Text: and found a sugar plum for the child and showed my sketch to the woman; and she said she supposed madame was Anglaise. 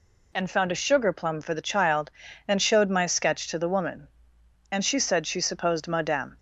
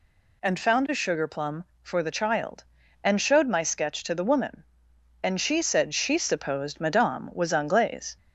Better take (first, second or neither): second